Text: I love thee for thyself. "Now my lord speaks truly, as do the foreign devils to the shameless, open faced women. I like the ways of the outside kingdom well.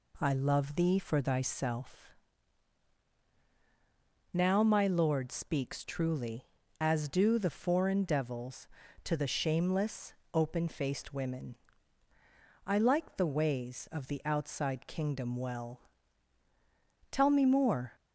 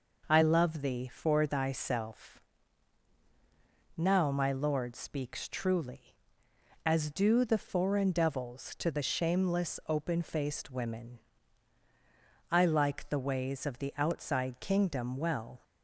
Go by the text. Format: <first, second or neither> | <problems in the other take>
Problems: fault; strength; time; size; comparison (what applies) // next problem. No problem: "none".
second | goes on to say "Tell me more"; noticeable; from 17.1 s on; 0.80 s long